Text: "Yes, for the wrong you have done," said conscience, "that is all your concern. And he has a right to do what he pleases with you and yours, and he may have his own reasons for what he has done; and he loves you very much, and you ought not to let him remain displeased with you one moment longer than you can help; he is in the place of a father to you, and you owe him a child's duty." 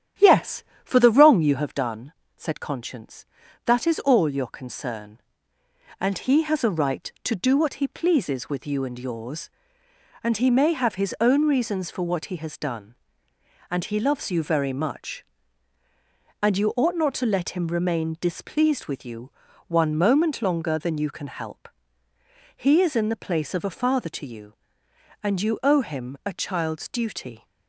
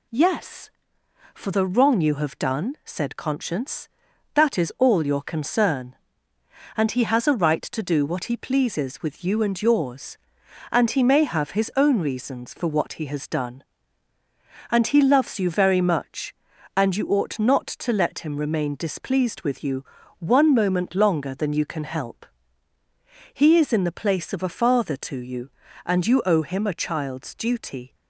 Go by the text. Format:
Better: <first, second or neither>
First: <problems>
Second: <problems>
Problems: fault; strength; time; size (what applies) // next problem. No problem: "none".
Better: second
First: starts louder than the rest; strong; until 1.8 s; 9.5 dB // pauses between "you" and "one"; at 19.3 s; 0.38 s long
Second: pauses between "you" and "one"; slight; at 19.8 s; 0.36 s long